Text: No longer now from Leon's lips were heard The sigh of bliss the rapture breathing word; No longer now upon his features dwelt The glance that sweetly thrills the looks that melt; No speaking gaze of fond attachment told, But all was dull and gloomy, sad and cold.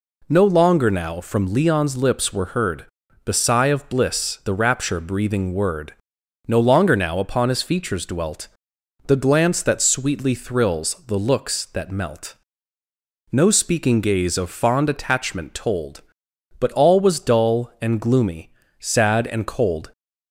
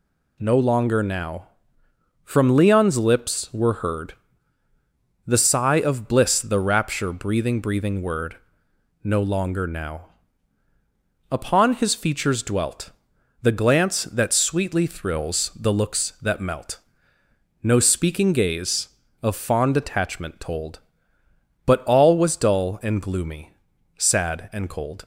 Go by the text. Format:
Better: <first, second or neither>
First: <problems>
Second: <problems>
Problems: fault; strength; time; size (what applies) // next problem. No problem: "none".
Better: first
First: pauses between "heard" and "The"; at 2.8 s; 0.40 s long // pauses between "dwelt" and "The"; noticeable; at 8.4 s; 0.60 s long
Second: pauses between "heard" and "The"; at 4.1 s; 1.1 s long // says "breathing" twice; at 7.5 s // pauses between "now" and "upon"; at 10.1 s; 1.1 s long // pauses between "dwelt" and "The"; noticeable; at 12.9 s; 0.50 s long